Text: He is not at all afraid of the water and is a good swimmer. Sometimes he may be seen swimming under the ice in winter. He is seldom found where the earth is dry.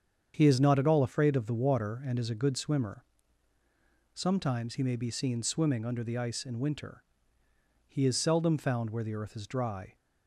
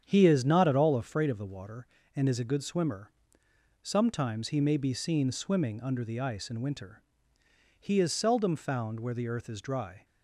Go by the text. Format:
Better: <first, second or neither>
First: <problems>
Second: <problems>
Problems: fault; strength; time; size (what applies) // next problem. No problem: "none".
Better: neither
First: starts louder than the rest; strong; until 1.3 s; 7.5 dB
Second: starts louder than the rest; strong; until 1.0 s; 8 dB